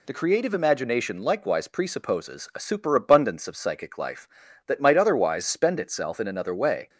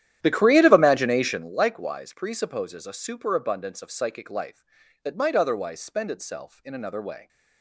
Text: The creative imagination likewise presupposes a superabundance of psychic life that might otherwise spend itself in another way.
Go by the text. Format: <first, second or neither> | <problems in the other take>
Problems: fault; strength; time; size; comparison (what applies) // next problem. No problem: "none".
first | starts louder than the rest; strong; until 1.6 s; 11 dB